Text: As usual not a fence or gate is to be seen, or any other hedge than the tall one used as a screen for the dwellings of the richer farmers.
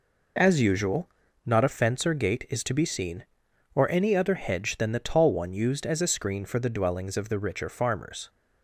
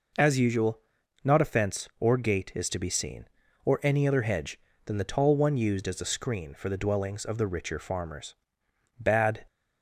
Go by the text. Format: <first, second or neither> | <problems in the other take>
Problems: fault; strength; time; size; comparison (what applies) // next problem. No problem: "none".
first | pauses between "usual" and "not"; at 0.7 s; 0.44 s long; also in the first // goes on to say "Bad"; slight; from 8.9 s on; 0.46 s long